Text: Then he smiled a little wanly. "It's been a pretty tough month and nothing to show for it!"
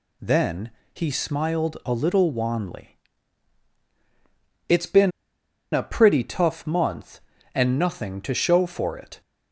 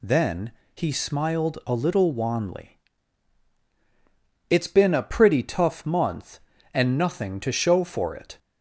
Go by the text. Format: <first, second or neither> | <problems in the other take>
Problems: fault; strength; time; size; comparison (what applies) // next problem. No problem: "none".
second | pauses between "Then" and "he"; slight; at 0.7 s; 0.22 s long; slight in the second // pauses between "been" and "a"; noticeable; at 5.1 s; 0.63 s long